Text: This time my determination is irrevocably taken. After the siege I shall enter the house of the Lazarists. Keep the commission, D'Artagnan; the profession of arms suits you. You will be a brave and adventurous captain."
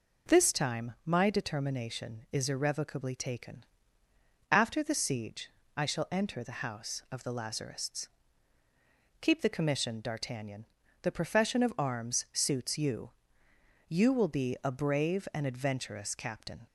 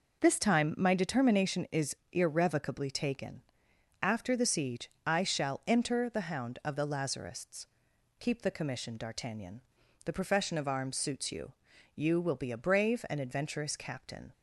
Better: first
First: pauses between "siege" and "I"; slight; at 5.4 s; 0.28 s long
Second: pauses between "is" and "irrevocably"; slight; at 1.9 s; 0.16 s long // pauses between "siege" and "I"; slight; at 4.8 s; 0.18 s long // says "hound" for "house"; at 6.2 s

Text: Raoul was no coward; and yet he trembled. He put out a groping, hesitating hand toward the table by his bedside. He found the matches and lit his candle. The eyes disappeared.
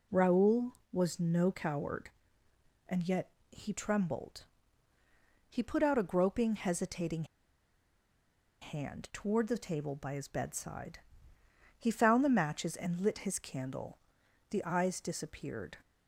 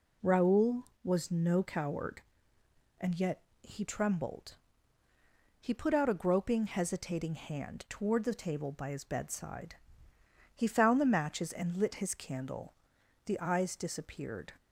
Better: second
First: pauses between "yet" and "he"; slight; at 3.3 s; 0.20 s long // pauses between "hesitating" and "hand"; strong; at 7.2 s; 1.3 s long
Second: pauses between "yet" and "he"; slight; at 3.4 s; 0.20 s long

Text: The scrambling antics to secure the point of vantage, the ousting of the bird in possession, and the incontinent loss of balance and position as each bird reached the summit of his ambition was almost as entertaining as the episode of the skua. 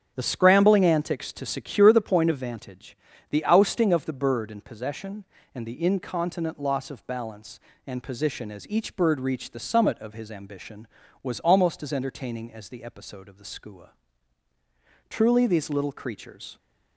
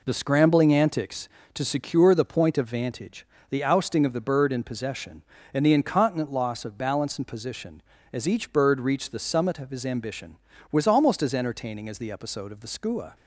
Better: second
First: starts louder than the rest; strong; until 1.1 s; 7 dB // goes on to say "Truly these little creatures"; from 15.0 s on; 1.4 s long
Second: none

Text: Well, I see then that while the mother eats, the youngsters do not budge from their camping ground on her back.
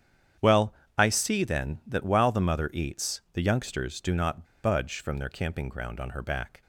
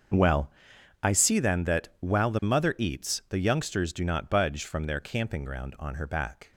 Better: second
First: starts louder than the rest; strong; until 1.6 s; 9 dB // pauses between "not" and "budge"; slight; at 4.4 s; 0.19 s long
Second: starts louder than the rest; until 1.6 s; 6.5 dB

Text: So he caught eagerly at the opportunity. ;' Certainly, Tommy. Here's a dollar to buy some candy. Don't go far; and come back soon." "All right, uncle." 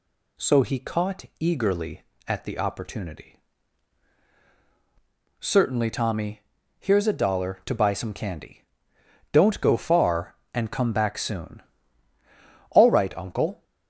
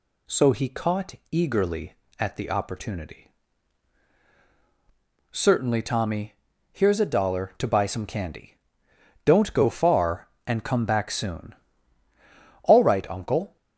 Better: neither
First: pauses between "caught" and "eagerly"; slight; at 1.2 s; 0.16 s long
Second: pauses between "caught" and "eagerly"; slight; at 1.1 s; 0.18 s long

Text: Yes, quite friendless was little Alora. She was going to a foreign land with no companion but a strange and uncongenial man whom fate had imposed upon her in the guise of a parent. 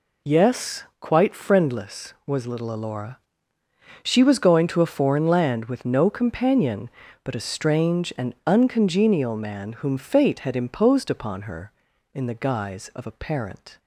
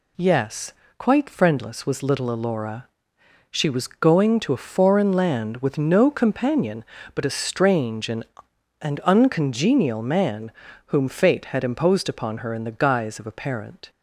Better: first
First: none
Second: says "and" twice; at 8.8 s // pauses between "man" and "whom"; slight; at 10.5 s; 0.34 s long

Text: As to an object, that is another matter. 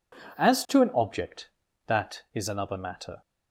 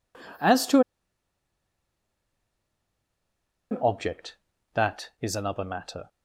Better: first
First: none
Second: pauses between "to" and "an"; strong; at 0.7 s; 2.9 s long

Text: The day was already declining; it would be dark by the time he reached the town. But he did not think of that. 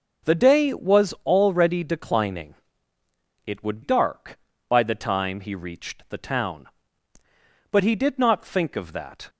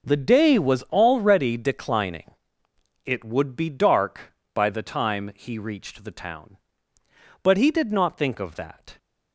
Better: second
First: skips "be"; at 3.8 s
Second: none

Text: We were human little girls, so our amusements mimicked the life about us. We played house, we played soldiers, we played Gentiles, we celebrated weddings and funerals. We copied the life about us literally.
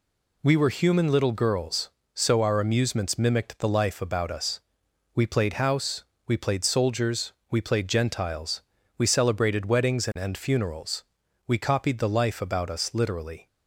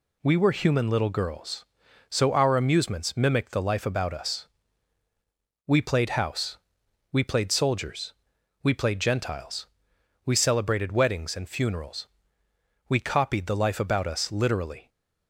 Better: second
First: says "and" twice; at 10.1 s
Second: none

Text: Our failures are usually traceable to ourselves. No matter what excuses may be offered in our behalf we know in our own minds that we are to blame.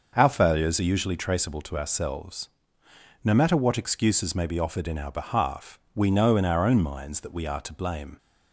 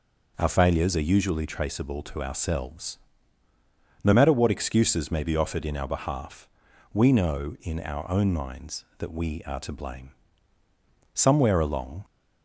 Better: first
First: pauses between "behalf" and "we"; slight; at 5.7 s; 0.16 s long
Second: pauses between "behalf" and "we"; noticeable; at 6.4 s; 0.46 s long // goes on to say "Somewhere along"; noticeable; from 11.1 s on; 0.92 s long

